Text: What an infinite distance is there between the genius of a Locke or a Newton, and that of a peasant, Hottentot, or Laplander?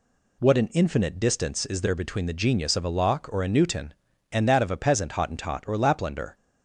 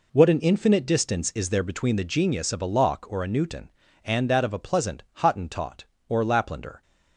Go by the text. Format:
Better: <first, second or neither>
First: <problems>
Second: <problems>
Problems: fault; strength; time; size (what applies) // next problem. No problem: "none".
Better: first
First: none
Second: says "pleasant" for "peasant"; at 4.5 s